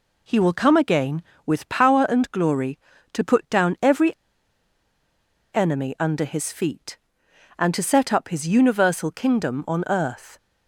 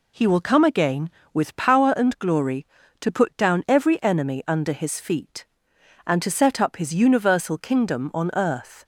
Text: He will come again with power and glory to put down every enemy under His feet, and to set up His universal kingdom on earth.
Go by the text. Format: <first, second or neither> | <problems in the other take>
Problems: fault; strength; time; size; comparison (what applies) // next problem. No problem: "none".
second | pauses between "every" and "enemy"; strong; at 4.1 s; 1.4 s long